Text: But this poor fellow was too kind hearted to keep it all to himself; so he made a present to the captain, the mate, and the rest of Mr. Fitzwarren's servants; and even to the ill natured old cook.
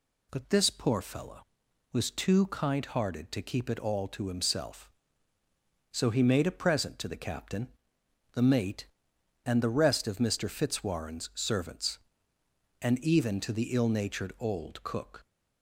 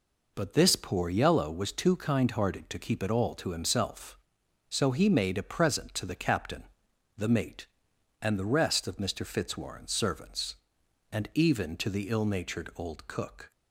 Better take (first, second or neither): first